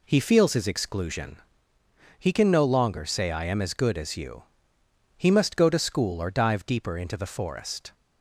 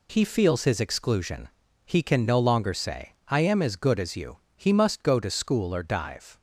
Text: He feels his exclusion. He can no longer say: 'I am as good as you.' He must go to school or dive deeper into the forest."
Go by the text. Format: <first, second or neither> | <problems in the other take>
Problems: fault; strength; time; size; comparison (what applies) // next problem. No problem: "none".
first | stops before "deeper into the forest"; at 6.3 s